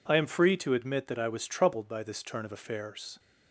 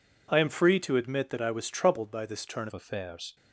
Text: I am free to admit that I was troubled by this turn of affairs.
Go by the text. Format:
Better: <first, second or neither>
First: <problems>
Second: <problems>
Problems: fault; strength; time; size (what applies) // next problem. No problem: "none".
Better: first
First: none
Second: changes voice at "of"; from 2.6 s on; 0.7 s long